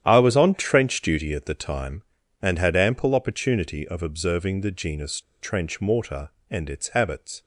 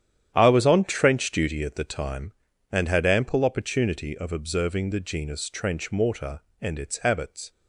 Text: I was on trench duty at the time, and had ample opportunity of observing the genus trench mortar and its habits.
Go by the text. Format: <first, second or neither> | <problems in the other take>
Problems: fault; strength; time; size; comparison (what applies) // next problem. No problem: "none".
second | starts louder than the rest; strong; until 1.0 s; 10 dB; strong in the second // pauses between "genus" and "trench"; slight; at 5.2 s; 0.20 s long